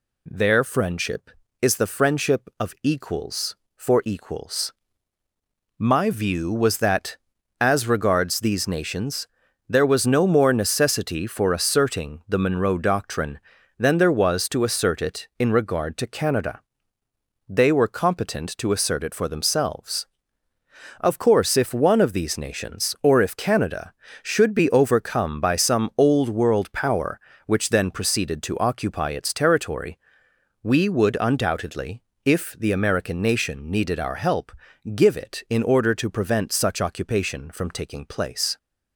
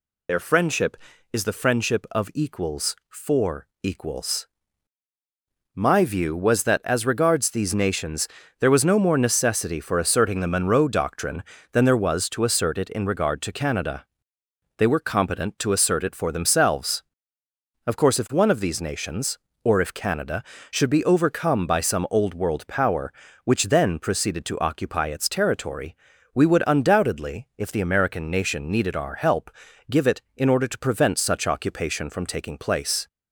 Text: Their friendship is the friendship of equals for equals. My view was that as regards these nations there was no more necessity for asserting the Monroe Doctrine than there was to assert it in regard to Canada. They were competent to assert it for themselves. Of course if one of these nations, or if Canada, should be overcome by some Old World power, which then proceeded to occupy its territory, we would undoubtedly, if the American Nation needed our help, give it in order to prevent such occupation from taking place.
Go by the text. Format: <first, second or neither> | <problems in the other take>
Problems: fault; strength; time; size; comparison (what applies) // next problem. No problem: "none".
first | loses the start of "Their"; at 0.2 s; 45 ms // pauses between "nations" and "there"; slight; at 8.2 s; 0.32 s long; also in the first